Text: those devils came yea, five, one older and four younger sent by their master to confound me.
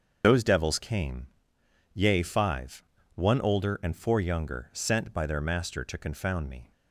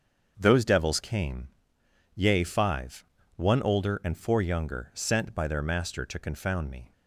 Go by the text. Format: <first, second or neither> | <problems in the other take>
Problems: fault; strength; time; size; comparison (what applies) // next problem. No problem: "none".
second | loses the start of "those"; at 0.2 s; 90 ms // starts louder than the rest; until 1.2 s; 6.5 dB; also in the second // pauses between "came" and "yea"; noticeable; at 1.2 s; 0.66 s long; noticeable in the second